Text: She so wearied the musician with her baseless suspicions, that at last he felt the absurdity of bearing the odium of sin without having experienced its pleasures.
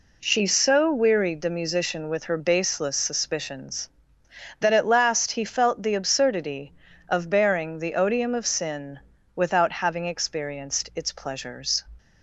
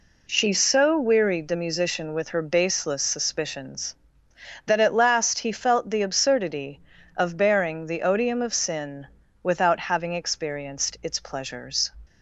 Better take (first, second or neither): neither